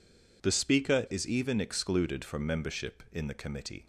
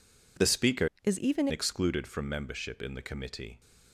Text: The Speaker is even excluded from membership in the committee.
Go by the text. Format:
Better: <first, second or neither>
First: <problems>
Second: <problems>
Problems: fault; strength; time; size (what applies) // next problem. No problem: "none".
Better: first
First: none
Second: changes voice from "is" to "even"; from 1.0 to 1.4 s; 0.4 s long